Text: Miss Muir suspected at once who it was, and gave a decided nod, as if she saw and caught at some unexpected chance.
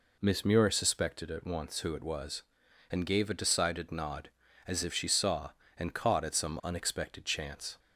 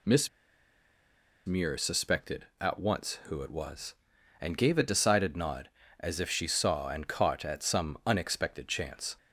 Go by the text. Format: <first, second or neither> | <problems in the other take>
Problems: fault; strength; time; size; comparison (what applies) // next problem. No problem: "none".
first | pauses between "Miss" and "Muir"; at 0.2 s; 1.1 s long